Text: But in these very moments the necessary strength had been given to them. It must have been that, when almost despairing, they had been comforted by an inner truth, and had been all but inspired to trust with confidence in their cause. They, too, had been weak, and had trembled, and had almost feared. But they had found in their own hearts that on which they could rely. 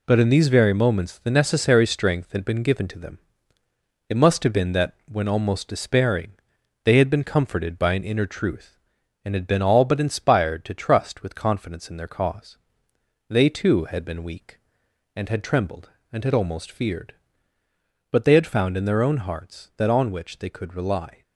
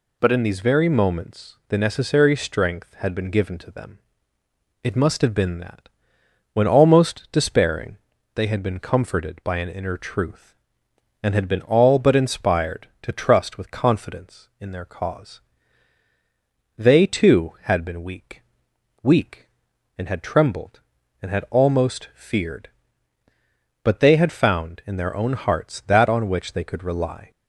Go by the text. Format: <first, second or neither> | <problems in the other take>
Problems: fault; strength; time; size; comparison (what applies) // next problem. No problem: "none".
first | says "weak" twice; at 19.0 s